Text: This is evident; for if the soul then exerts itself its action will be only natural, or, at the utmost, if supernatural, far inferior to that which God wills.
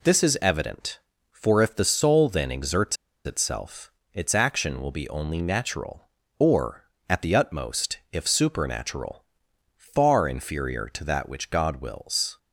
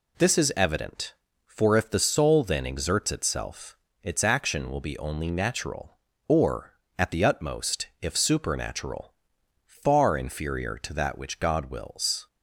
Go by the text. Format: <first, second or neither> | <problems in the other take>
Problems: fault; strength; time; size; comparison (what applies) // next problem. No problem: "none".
second | pauses between "exerts" and "itself"; slight; at 2.9 s; 0.29 s long // pauses between "itself" and "its"; slight; at 3.8 s; 0.24 s long; slight in the second